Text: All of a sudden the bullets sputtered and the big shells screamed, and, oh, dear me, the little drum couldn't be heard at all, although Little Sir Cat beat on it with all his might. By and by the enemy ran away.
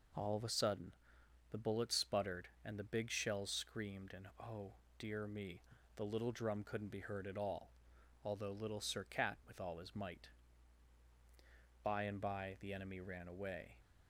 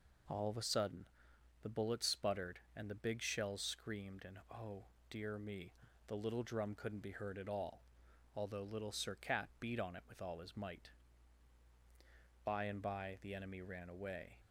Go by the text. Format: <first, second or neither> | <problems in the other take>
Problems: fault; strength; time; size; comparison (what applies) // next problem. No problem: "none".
second | pauses between "sudden" and "the"; noticeable; at 0.9 s; 0.58 s long; noticeable in the second // skips "beat on it"; at 9.4 s